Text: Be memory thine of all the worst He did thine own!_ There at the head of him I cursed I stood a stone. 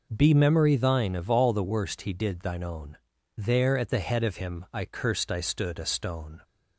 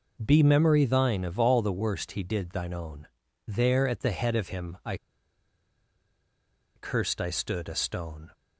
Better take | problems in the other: first | pauses between "I" and "cursed"; strong; at 4.9 s; 1.7 s long

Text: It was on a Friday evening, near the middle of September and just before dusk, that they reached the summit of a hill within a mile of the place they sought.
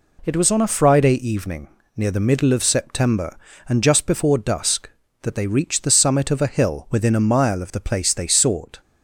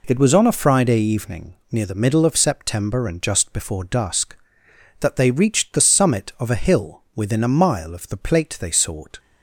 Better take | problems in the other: first | says "plate" for "place"; at 8.1 s

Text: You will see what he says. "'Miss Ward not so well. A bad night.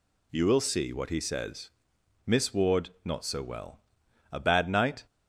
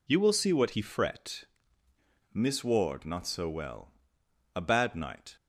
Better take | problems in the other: first | says "fret" for "says"; at 0.7 s

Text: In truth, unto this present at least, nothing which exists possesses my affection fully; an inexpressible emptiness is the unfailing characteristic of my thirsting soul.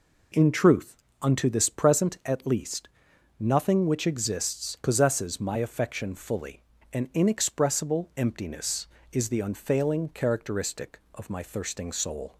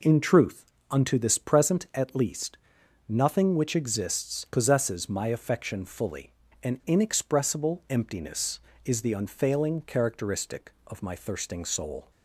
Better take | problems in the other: neither | none

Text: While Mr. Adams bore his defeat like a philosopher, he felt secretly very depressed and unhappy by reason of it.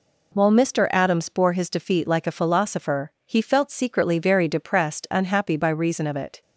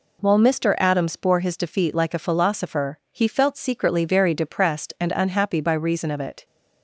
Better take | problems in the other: second | skips "and"; at 5.0 s

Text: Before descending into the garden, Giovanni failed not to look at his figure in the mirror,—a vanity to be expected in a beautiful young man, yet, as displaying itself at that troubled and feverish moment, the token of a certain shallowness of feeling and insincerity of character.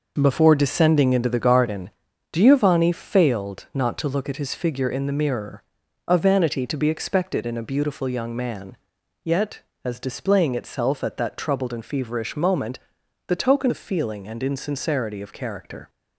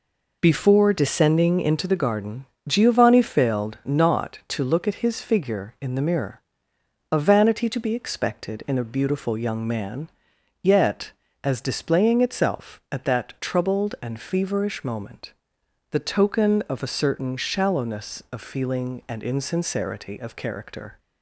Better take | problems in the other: second | skips "of a certain shallowness"; at 13.6 s

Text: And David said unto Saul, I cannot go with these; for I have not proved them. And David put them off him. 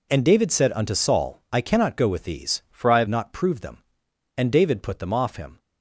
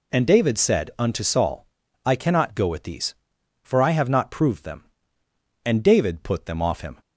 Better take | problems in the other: second | changes voice from "for" to "have"; from 2.7 to 3.0 s; 0.3 s long

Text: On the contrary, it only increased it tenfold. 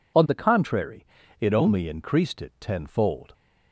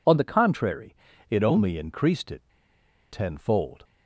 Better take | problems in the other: first | pauses between "it" and "tenfold"; noticeable; at 2.4 s; 0.71 s long

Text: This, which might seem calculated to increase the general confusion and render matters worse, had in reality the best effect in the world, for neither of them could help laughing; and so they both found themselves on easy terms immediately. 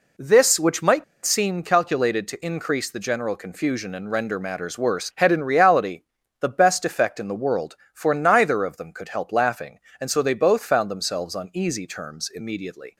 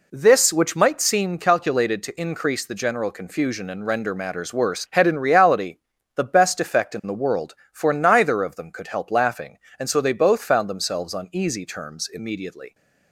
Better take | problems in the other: second | pauses between "might" and "seem"; slight; at 1.0 s; 0.21 s long // pauses between "reality" and "the"; slight; at 6.0 s; 0.36 s long; slight in the second

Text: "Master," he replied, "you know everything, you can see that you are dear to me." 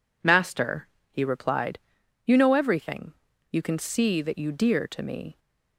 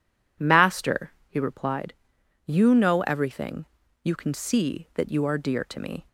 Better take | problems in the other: second | skips "are"; at 4.5 s

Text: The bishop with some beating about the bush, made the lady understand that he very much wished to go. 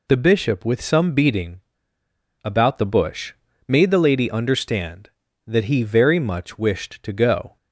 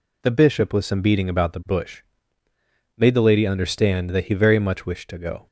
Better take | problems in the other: second | pauses between "beating" and "about"; noticeable; at 1.6 s; 0.81 s long

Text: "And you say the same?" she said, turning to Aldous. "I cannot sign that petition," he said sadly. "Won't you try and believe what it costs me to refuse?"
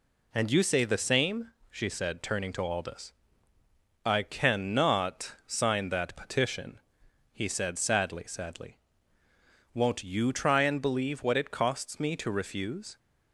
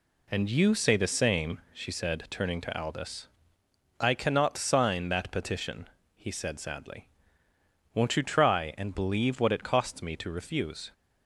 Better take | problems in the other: second | says "sadly" twice; at 8.2 s

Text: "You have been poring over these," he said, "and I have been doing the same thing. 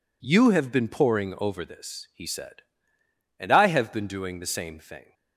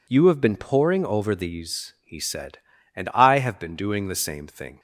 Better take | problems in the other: second | says "this" for "these"; at 1.6 s

